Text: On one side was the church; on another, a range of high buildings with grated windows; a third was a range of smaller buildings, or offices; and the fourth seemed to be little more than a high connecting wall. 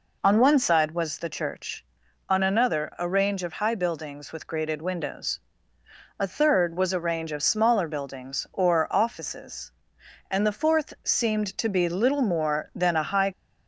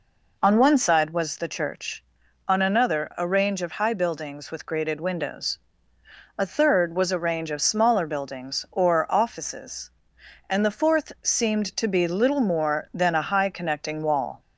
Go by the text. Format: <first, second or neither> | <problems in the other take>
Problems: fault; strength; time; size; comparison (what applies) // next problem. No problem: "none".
second | stops before "connecting wall"; at 13.3 s